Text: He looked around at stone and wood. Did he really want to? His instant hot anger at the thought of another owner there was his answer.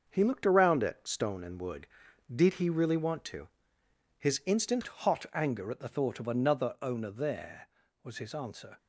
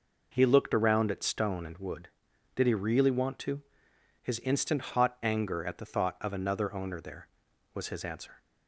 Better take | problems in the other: second | starts louder than the rest; until 1.0 s; 6.5 dB // changes voice at "hot"; from 4.8 s on; 3.9 s long

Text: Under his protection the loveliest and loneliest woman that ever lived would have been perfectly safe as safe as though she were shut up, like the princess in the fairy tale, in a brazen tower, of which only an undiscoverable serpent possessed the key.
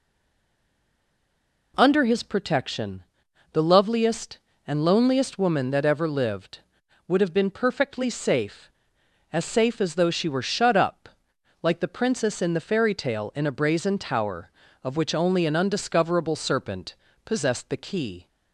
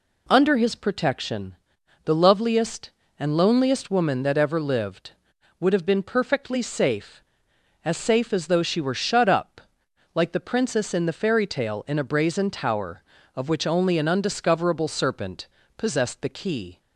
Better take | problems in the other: second | stays silent before the first word; noticeable; until 1.7 s; 1.7 s long // pauses between "protection" and "the"; noticeable; at 3.0 s; 0.48 s long; noticeable in the second // pauses between "serpent" and "possessed"; slight; at 16.9 s; 0.30 s long; slight in the second

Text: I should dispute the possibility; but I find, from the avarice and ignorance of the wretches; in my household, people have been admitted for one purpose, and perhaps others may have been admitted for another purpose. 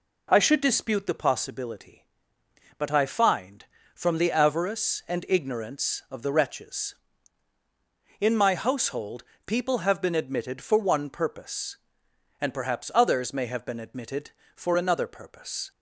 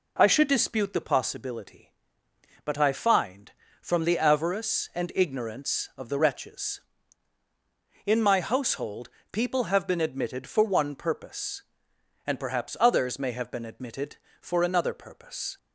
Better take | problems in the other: neither | none

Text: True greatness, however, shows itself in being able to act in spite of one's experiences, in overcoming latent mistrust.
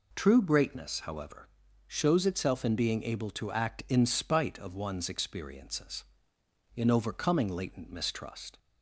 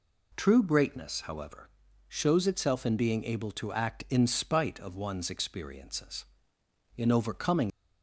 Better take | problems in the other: first | stops before "latent mistrust"; at 7.6 s

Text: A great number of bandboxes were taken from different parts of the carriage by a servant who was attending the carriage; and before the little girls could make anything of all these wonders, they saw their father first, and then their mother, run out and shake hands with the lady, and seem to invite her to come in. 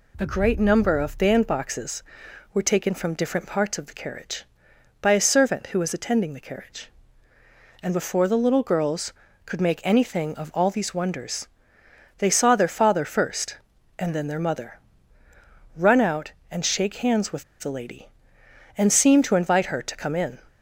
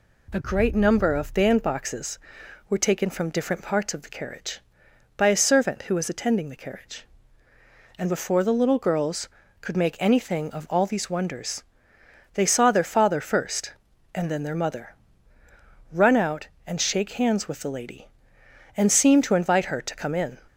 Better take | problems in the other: second | pauses between "with" and "the"; slight; at 17.4 s; 0.16 s long

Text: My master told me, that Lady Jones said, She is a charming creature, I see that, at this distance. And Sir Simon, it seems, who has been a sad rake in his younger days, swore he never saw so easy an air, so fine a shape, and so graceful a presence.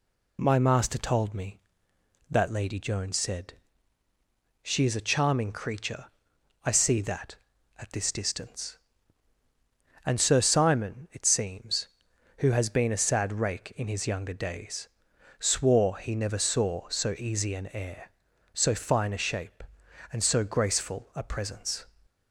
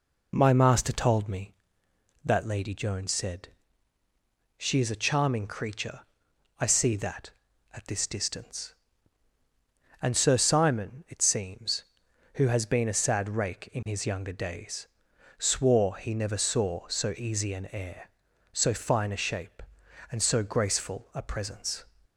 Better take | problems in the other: first | starts louder than the rest; until 1.5 s; 3.5 dB

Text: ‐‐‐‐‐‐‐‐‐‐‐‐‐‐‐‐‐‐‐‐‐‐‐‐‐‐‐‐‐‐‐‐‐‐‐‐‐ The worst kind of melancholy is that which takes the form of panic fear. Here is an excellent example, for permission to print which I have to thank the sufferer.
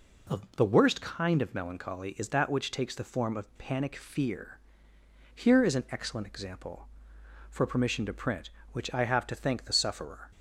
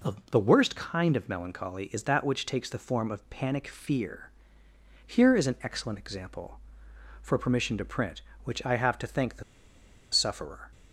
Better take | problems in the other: first | pauses between "the" and "sufferer"; noticeable; at 9.4 s; 0.69 s long

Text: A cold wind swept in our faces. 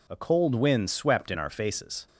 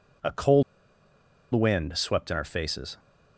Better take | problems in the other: first | pauses between "cold" and "wind"; noticeable; at 0.6 s; 0.91 s long

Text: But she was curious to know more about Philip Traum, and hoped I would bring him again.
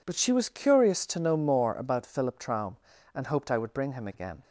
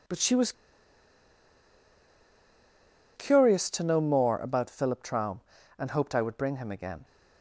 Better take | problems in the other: first | pauses between "was" and "curious"; strong; at 0.5 s; 2.6 s long

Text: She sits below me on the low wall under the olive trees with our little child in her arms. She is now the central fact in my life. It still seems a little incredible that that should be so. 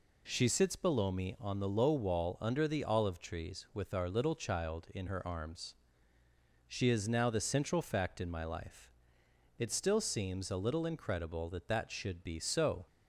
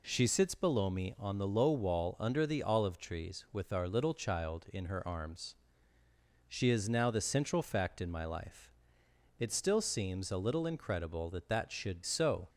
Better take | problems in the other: first | skips "be"; at 12.0 s

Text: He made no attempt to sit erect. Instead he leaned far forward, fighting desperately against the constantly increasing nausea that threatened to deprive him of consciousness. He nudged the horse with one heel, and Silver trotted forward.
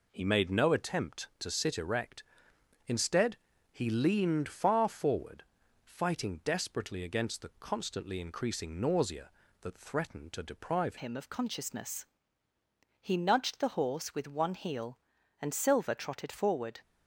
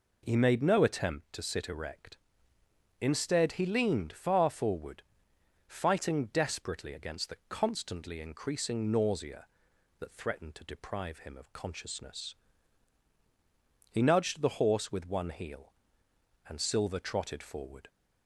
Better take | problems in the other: second | pauses between "Instead" and "he"; slight; at 3.3 s; 0.36 s long // changes voice at "him"; from 10.9 s on; 5.9 s long

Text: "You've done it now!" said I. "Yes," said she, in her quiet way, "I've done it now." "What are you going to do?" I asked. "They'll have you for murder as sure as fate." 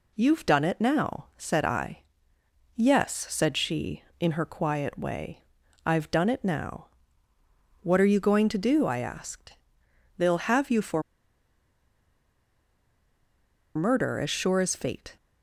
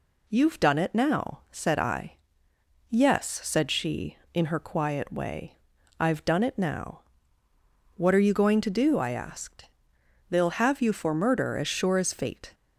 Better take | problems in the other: second | pauses between "for" and "murder"; strong; at 11.0 s; 2.7 s long

